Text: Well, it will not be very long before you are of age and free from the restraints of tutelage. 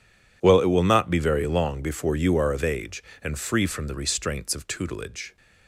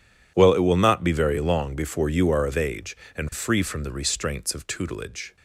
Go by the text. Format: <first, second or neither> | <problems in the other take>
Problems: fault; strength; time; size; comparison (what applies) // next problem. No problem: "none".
neither | none